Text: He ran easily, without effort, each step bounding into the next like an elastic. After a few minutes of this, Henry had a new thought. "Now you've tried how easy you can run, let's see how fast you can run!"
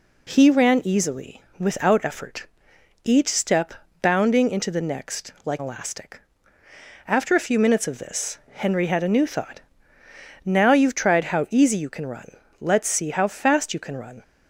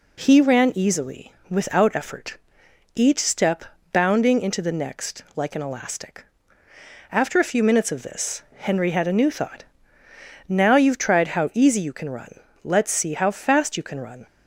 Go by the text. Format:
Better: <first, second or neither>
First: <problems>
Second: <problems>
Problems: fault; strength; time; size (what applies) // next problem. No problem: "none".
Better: second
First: pauses between "step" and "bounding"; slight; at 3.7 s; 0.30 s long // skips "an"; at 5.5 s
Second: pauses between "step" and "bounding"; slight; at 3.6 s; 0.30 s long